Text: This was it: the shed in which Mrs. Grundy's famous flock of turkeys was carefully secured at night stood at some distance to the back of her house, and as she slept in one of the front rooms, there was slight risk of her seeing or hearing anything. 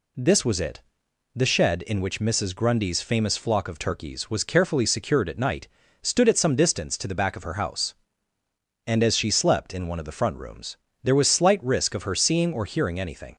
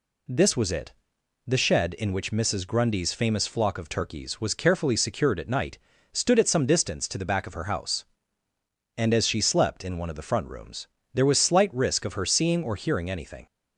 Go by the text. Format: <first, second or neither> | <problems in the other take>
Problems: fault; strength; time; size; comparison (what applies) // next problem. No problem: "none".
neither | pauses between "night" and "stood"; slight; the same in both